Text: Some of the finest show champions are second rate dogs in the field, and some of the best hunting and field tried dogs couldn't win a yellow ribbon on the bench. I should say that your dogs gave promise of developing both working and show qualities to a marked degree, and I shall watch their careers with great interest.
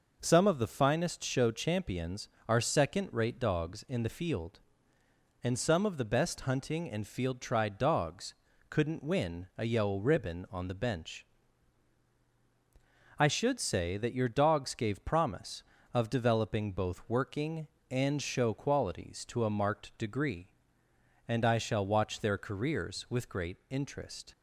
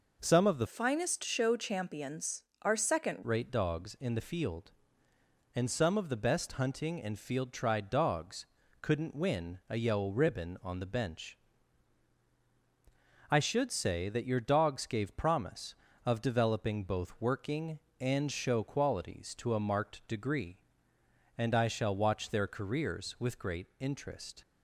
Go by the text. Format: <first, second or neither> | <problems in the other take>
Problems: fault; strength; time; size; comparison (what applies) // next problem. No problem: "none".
first | changes voice from "finest" to "second"; from 0.6 to 3.2 s; 2.6 s long // pauses between "dogs" and "couldn't"; slight; at 8.4 s; 0.34 s long; slight in the first